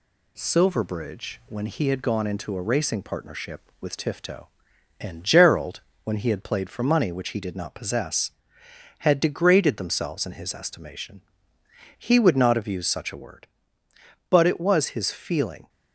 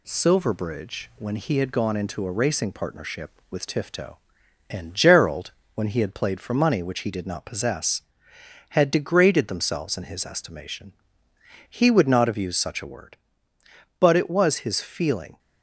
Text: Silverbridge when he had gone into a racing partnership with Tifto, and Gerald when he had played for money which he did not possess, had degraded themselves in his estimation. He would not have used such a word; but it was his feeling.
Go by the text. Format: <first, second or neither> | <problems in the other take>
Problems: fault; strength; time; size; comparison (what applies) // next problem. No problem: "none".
neither | pauses between "Gerald" and "when"; slight; the same in both